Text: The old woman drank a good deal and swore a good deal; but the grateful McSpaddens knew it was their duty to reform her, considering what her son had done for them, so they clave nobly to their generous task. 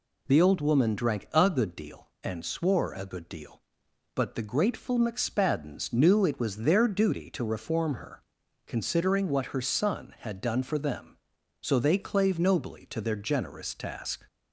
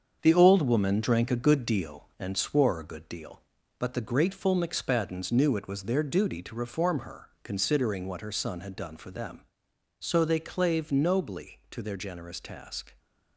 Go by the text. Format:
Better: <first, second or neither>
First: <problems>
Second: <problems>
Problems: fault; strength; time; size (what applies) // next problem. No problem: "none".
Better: first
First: none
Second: gets quieter; throughout; 7 dB